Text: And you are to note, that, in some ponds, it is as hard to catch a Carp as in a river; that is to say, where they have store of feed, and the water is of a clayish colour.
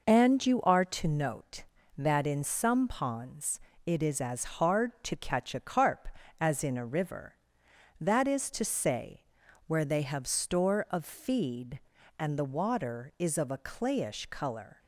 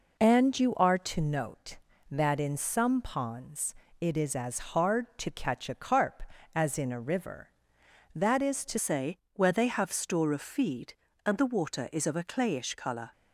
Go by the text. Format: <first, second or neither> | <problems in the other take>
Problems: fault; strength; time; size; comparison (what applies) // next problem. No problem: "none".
first | changes voice at "say"; from 8.7 s on; 4.4 s long